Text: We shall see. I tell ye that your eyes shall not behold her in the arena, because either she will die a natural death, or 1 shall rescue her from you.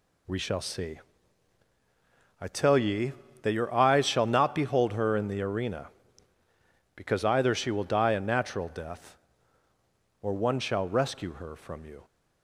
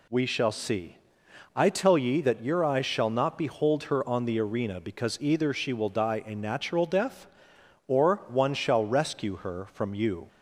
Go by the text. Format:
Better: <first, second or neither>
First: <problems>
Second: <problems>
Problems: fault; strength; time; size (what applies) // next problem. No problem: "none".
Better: first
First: none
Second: says "on" for "in"; at 4.0 s